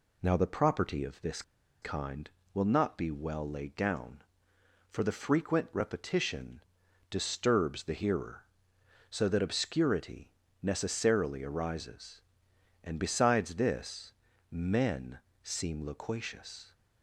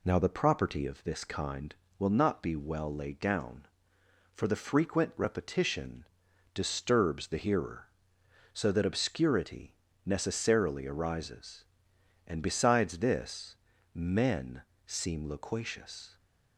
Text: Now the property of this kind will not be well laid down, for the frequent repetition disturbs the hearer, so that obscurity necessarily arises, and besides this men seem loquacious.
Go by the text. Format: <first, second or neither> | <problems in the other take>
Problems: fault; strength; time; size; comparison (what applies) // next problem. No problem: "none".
second | pauses between "this" and "kind"; at 1.4 s; 0.40 s long // pauses between "repetition" and "disturbs"; noticeable; at 6.6 s; 0.50 s long; noticeable in the second // pauses between "obscurity" and "necessarily"; slight; at 10.3 s; 0.32 s long; slight in the second // pauses between "this" and "men"; at 14.1 s; 0.38 s long; also in the second // pauses between "men" and "seem"; slight; at 15.1 s; 0.24 s long; slight in the second